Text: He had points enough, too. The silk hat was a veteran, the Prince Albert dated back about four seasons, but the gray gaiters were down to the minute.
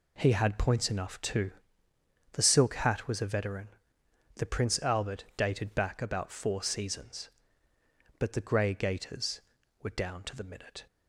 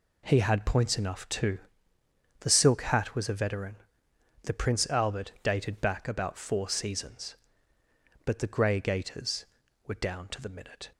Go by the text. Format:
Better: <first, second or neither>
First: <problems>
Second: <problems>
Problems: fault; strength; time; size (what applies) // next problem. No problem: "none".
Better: neither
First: none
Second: none